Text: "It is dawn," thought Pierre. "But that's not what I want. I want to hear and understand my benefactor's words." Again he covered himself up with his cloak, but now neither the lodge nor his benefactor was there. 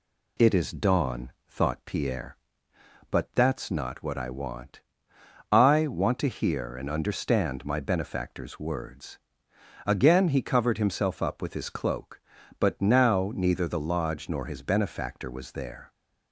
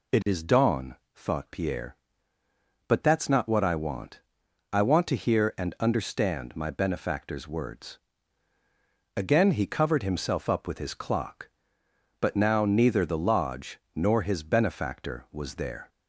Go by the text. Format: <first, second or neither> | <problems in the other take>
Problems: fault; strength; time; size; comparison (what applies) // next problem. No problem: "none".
first | says "clock" for "cloak"; at 10.9 s // pauses between "lodge" and "nor"; slight; at 13.7 s; 0.16 s long